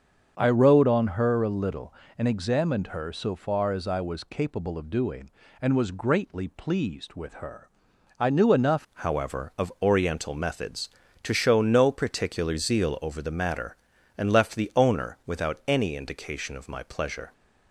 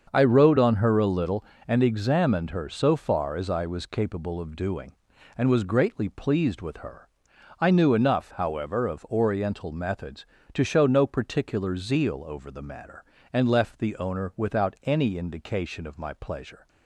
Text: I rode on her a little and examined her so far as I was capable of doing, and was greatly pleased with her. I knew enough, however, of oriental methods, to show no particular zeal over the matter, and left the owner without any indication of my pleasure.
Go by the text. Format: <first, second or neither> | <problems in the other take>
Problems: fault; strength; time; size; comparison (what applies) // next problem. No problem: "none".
second | starts louder than the rest; until 1.3 s; 7 dB; also in the second // changes voice at "however"; from 8.9 s on; 8.4 s long